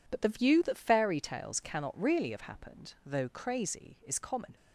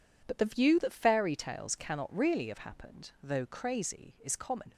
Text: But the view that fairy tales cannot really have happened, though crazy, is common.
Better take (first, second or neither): neither